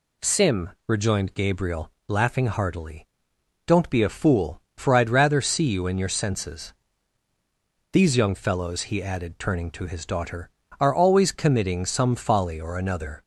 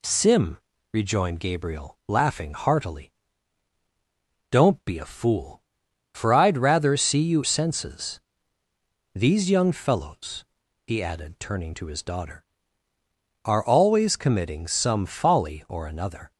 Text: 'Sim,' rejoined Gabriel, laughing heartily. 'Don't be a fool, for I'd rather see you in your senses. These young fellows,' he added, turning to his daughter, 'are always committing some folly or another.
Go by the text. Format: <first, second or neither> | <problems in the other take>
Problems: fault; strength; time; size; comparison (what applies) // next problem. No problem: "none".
first | skips "in your"; at 7.4 s